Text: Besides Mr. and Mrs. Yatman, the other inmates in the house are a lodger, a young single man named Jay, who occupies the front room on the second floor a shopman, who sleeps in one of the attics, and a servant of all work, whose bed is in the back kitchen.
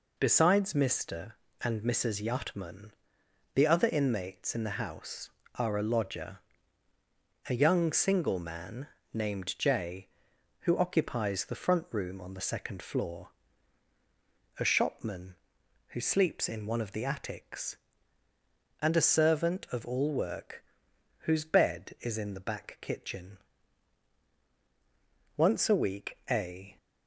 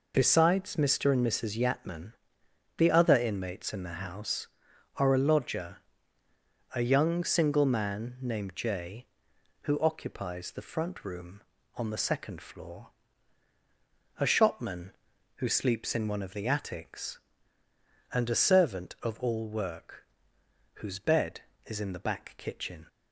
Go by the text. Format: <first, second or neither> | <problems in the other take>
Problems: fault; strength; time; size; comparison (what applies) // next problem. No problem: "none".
second | pauses between "man" and "named"; slight; at 8.8 s; 0.26 s long // pauses between "floor" and "a"; strong; at 13.2 s; 1.3 s long; strong in the second // goes on to say "Once a week a"; from 25.3 s on; 1.4 s long